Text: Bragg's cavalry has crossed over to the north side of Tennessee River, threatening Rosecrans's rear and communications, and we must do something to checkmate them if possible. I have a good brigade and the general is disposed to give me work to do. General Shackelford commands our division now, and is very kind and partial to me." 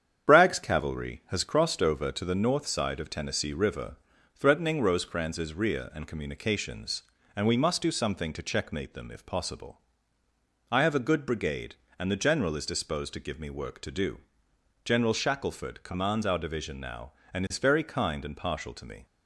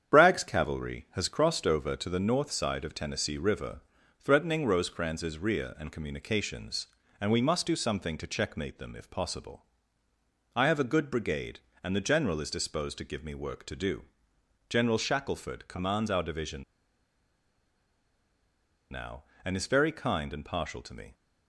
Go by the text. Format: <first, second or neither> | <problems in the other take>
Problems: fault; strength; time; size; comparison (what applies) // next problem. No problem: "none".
first | starts louder than the rest; strong; until 1.1 s; 8.5 dB; strong in the first // pauses between "division" and "now"; strong; at 16.6 s; 2.2 s long